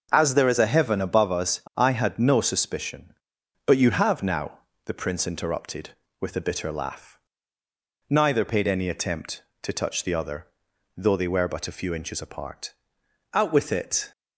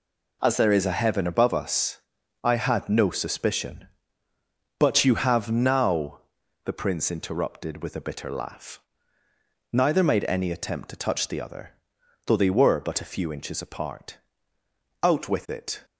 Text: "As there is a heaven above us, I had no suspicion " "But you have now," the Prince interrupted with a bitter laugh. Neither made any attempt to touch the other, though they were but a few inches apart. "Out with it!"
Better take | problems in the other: second | says "paid" for "made"; at 8.4 s

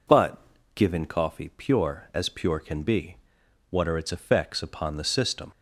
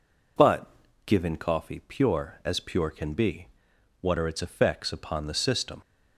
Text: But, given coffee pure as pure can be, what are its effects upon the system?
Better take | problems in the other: neither | none

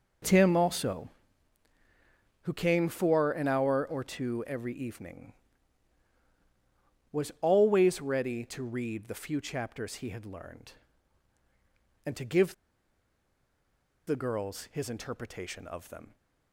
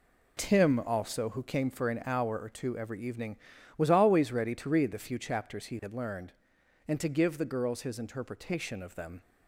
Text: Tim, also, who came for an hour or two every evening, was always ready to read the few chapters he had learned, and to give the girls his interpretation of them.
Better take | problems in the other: second | pauses between "give" and "the"; strong; at 12.5 s; 1.5 s long

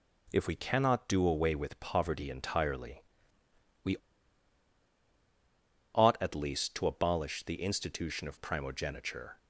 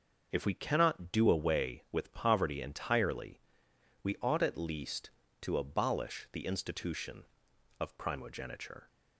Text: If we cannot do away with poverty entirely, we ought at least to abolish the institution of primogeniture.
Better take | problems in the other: second | pauses between "we" and "ought"; strong; at 3.9 s; 1.9 s long

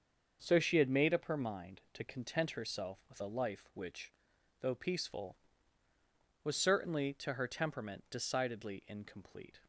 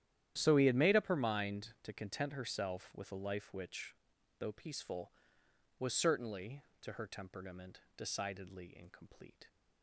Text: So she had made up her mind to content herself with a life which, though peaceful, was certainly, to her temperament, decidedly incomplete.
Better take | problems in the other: first | starts louder than the rest; strong; until 1.3 s; 11 dB; also in the first // says "he" for "she"; at 0.5 s

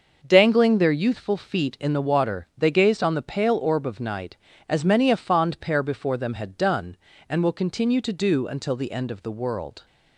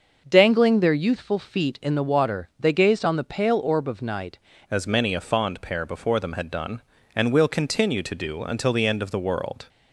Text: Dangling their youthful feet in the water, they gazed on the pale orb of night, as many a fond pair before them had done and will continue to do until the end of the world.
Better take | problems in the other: first | starts louder than the rest; until 1.3 s; 6 dB; also in the first // changes voice at "as"; from 4.7 s on; 4.9 s long

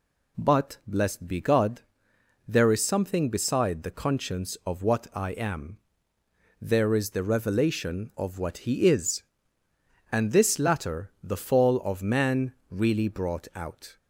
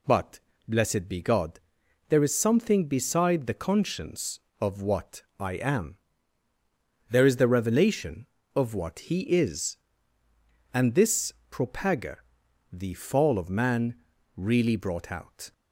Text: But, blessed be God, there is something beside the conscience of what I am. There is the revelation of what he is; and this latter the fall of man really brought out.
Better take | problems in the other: first | pauses between "what" and "I"; slight; at 5.2 s; 0.18 s long // says "propaga" for "latter"; at 11.5 s // pauses between "man" and "really"; at 13.9 s; 0.42 s long; slight in the first

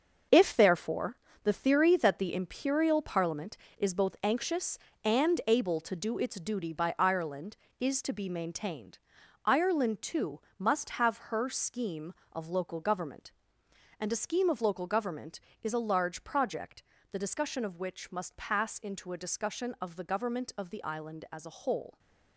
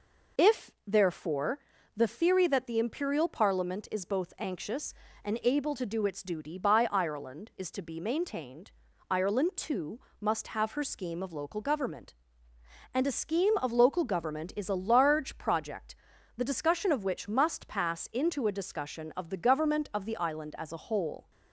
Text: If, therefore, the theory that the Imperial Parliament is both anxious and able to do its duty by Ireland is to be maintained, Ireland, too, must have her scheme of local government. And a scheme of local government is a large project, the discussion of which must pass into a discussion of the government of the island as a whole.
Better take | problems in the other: second | gets quieter; strong; throughout; 9 dB

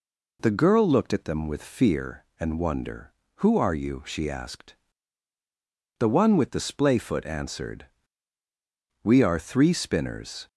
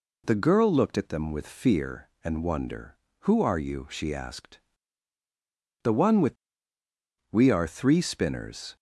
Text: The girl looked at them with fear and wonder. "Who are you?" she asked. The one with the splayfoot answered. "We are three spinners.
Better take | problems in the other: first | skips "the splayfoot answered"; at 6.8 s

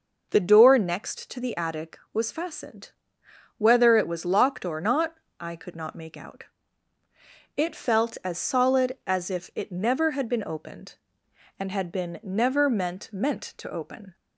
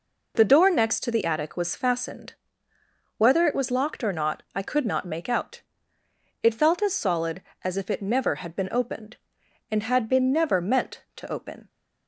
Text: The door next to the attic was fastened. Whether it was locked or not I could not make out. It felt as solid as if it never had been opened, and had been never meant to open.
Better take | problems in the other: second | pauses between "not" and "I"; slight; at 5.1 s; 0.24 s long // says "meant" twice; at 13.1 s

